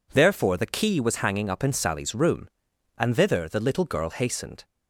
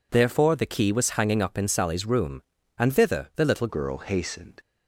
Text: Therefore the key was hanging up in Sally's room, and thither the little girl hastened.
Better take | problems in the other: first | changes voice at "girl"; from 3.6 s on; 0.9 s long

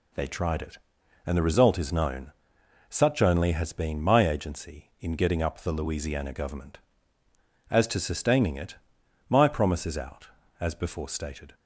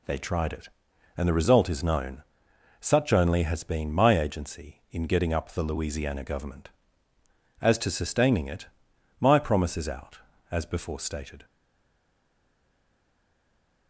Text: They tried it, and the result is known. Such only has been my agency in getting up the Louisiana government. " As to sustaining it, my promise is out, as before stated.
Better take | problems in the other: first | stays silent after the last word; from 11.4 s on; 2.4 s long

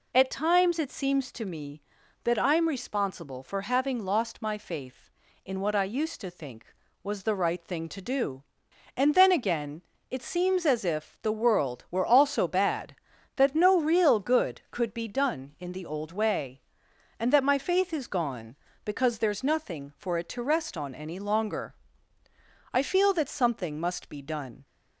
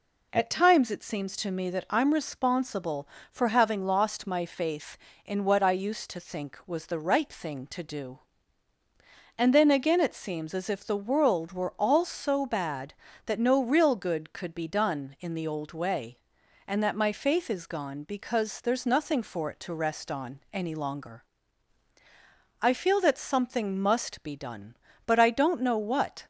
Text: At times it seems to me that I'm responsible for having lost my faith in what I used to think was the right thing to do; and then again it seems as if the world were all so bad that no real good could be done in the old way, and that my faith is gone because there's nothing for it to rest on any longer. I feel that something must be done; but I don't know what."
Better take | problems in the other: second | pauses between "again" and "it"; slight; at 9.8 s; 0.28 s long // stops before "but I don't know what"; at 24.6 s

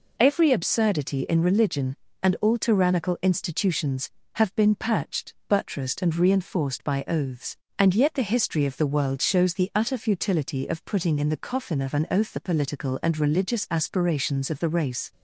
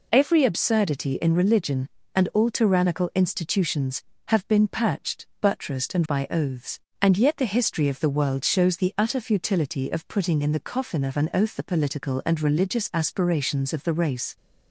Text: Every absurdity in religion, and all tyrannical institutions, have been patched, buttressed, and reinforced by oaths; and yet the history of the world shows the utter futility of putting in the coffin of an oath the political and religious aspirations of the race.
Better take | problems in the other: first | skips "reinforced"; at 6.0 s

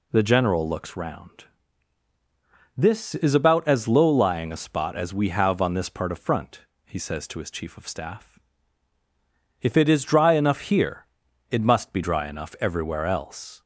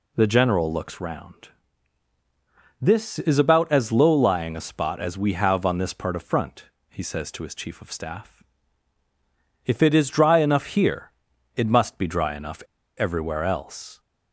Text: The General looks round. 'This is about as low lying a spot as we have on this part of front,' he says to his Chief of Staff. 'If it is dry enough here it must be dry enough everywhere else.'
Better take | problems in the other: first | pauses between "here" and "it"; at 11.1 s; 0.44 s long; also in the first // pauses between "enough" and "everywhere"; at 12.6 s; 0.36 s long

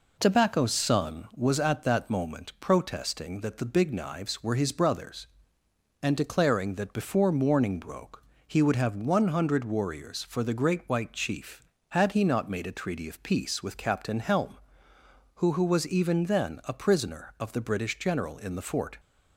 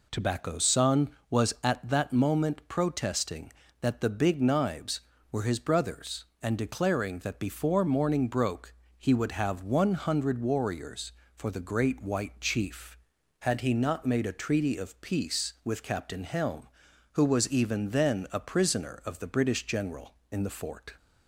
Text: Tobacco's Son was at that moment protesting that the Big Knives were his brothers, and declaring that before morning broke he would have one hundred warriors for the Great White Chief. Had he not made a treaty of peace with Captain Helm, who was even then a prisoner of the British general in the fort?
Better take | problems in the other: second | pauses between "broke" and "he"; slight; at 8.2 s; 0.24 s long; slight in the second // says "who" twice; at 15.5 s

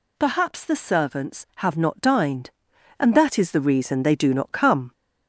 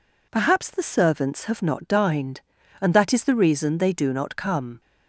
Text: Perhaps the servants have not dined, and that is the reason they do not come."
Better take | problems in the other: second | gets louder; slight; throughout; 3 dB

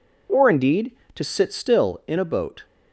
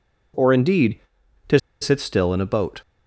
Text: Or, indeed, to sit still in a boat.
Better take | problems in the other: first | pauses between "to" and "sit"; slight; at 1.5 s; 0.22 s long

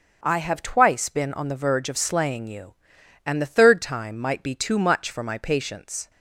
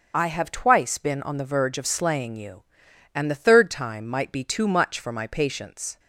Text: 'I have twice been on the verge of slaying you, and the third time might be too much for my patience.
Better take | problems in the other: first | loses the start of "I"; at 0.1 s; 35 ms // starts louder than the rest; until 1.1 s; 6.5 dB; also in the first

